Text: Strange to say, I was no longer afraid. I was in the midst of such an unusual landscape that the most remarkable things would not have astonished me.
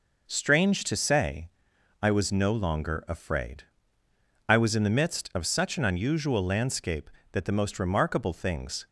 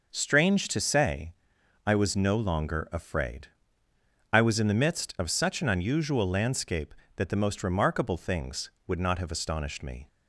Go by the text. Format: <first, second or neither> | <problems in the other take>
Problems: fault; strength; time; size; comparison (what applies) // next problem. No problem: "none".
second | stops before "would not have astonished me"; at 8.8 s